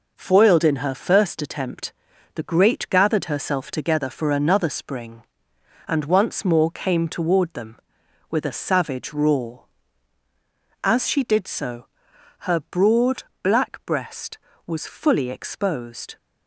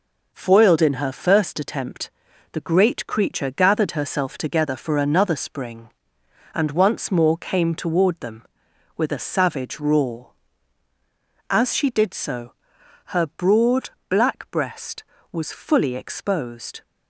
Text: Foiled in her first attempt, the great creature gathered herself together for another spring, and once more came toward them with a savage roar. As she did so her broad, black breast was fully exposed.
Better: second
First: skips "creature"; at 2.8 s // pauses between "so" and "her"; noticeable; at 11.8 s; 0.54 s long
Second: pauses between "so" and "her"; noticeable; at 12.5 s; 0.54 s long

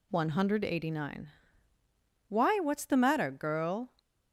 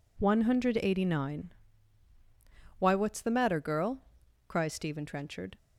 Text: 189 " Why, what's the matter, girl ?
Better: first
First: none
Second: goes on to say "cries Stephen Trenchard"; noticeable; from 4.4 s on; 1.1 s long

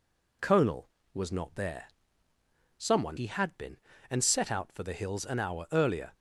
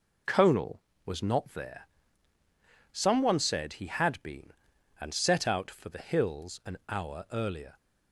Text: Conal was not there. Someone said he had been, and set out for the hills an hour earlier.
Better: second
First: skips "said"; at 3.1 s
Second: none

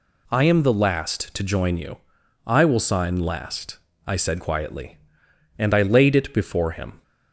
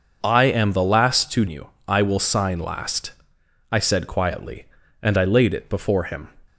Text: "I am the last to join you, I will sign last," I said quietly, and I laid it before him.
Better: first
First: none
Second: skips "join"; at 1.4 s

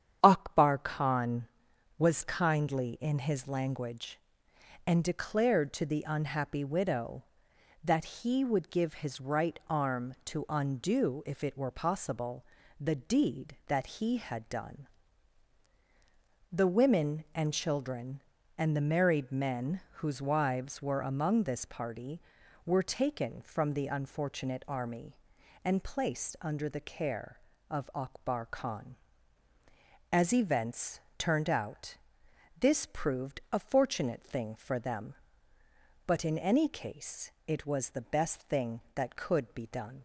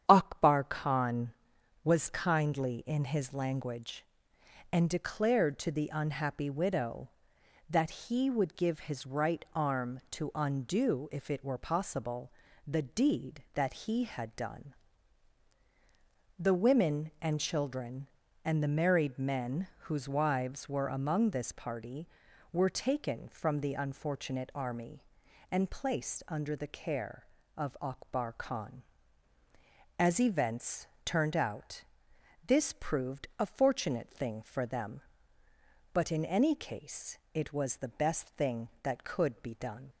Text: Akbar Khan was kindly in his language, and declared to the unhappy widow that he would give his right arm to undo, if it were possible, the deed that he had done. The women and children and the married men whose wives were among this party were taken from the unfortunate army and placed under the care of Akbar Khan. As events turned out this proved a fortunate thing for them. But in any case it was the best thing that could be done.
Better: neither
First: starts louder than the rest; strong; until 1.2 s; 9 dB // pauses between "events" and "turned"; slight; at 30.9 s; 0.20 s long // pauses between "out" and "this"; noticeable; at 31.9 s; 0.62 s long // pauses between "case" and "it"; slight; at 37.2 s; 0.16 s long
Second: starts louder than the rest; strong; until 1.0 s; 9 dB // pauses between "events" and "turned"; slight; at 30.8 s; 0.20 s long // pauses between "out" and "this"; noticeable; at 31.8 s; 0.62 s long // pauses between "case" and "it"; slight; at 37.1 s; 0.16 s long

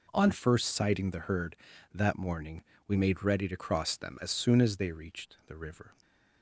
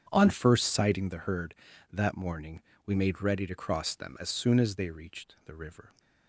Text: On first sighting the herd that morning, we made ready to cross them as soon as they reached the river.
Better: first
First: none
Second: starts louder than the rest; strong; until 1.0 s; 8.5 dB

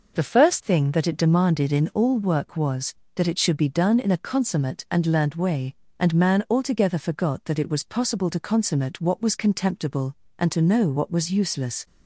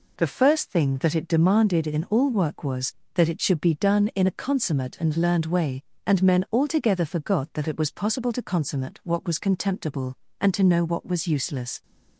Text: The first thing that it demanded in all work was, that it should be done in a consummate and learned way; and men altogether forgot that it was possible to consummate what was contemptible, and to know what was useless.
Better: second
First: says "man" for "men"; at 6.1 s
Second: none

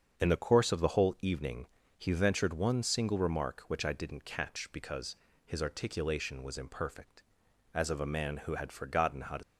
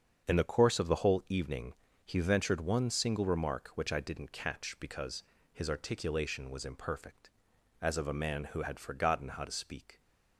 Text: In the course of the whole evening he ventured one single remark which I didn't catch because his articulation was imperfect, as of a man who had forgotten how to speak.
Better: second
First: starts louder than the rest; strong; until 1.2 s; 7 dB // pauses between "evening" and "he"; slight; at 1.6 s; 0.32 s long // pauses between "because" and "his"; slight; at 5.1 s; 0.30 s long // stops before "speak"; at 9.4 s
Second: starts louder than the rest; strong; until 1.3 s; 7 dB // pauses between "evening" and "he"; slight; at 1.7 s; 0.32 s long // pauses between "because" and "his"; slight; at 5.2 s; 0.30 s long

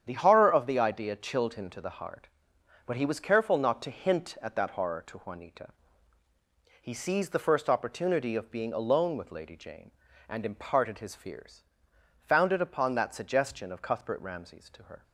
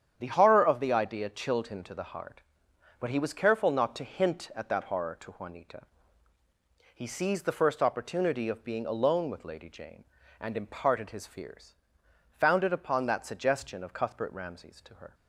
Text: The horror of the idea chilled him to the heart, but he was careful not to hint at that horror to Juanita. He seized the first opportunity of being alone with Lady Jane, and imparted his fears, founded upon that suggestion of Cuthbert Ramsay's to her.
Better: neither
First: starts louder than the rest; strong; until 1.0 s; 8.5 dB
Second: starts louder than the rest; strong; until 1.1 s; 8.5 dB

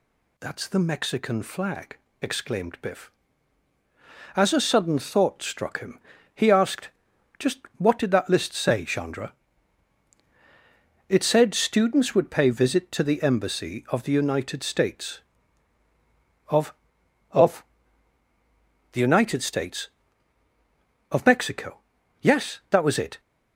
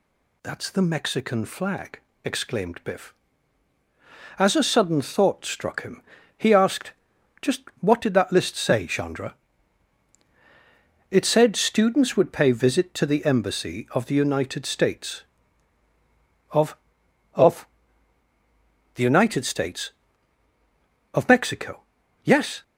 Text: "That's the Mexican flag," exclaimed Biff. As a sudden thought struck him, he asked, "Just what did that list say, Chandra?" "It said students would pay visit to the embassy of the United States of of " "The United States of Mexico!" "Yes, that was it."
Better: first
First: pauses between "Just" and "what"; slight; at 7.6 s; 0.18 s long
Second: pauses between "Just" and "what"; slight; at 7.6 s; 0.18 s long // stops before "that was it"; at 22.6 s

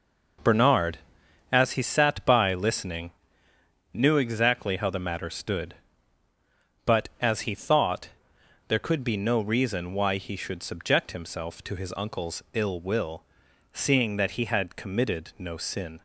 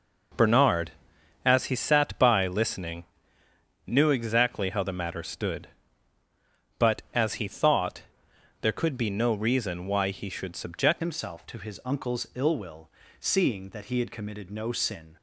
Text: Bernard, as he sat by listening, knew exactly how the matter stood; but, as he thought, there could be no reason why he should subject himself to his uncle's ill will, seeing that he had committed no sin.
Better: first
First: none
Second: changes voice at "himself"; from 11.0 s on; 4.1 s long

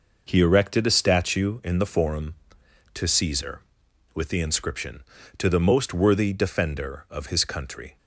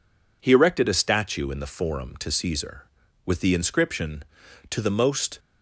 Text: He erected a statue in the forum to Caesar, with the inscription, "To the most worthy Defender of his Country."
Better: first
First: none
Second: stops before "worthy Defender of his Country"; at 5.3 s

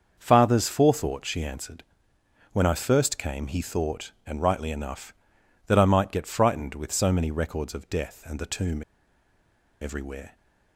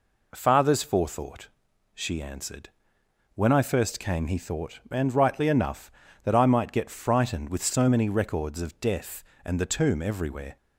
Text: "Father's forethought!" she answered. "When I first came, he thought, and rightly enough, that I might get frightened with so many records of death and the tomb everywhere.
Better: second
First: starts louder than the rest; until 1.2 s; 6.5 dB // pauses between "tomb" and "everywhere"; at 8.8 s; 0.98 s long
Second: none

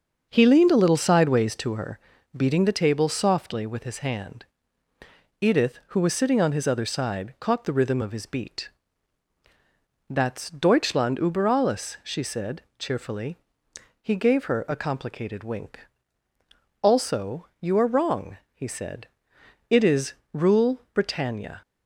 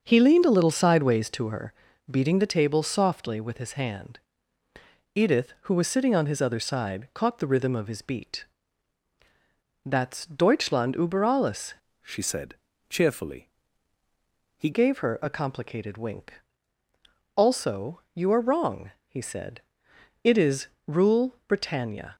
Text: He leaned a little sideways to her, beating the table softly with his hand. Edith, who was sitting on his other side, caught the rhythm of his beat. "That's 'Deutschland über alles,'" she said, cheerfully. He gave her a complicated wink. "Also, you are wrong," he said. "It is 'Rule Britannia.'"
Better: first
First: starts louder than the rest; until 1.3 s; 6.5 dB // pauses between "is" and "Rule"; slight; at 20.1 s; 0.20 s long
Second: starts louder than the rest; until 1.0 s; 6.5 dB // changes voice from "she" to "He"; from 12.0 to 14.7 s; 2.7 s long // pauses between "is" and "Rule"; slight; at 20.6 s; 0.20 s long

